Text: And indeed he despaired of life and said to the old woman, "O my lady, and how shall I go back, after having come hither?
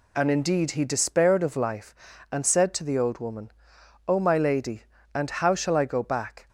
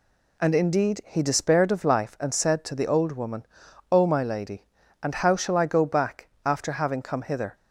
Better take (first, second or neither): second